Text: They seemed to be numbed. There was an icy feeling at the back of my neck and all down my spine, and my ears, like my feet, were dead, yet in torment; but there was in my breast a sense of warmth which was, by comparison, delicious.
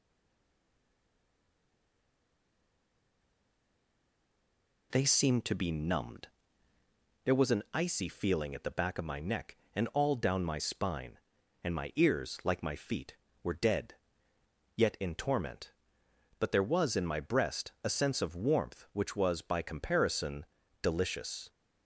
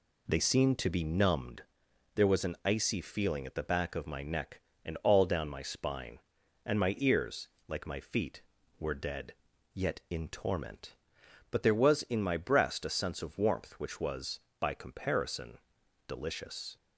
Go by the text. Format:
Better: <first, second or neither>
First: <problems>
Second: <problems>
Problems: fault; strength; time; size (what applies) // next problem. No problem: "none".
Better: second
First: stays silent before the first word; strong; until 4.9 s; 4.9 s long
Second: none